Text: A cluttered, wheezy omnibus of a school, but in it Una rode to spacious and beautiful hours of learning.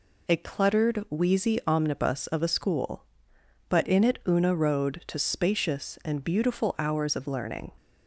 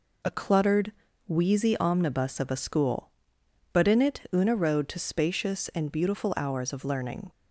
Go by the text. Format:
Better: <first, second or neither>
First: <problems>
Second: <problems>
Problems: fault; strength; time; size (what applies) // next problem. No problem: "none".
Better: neither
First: none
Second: none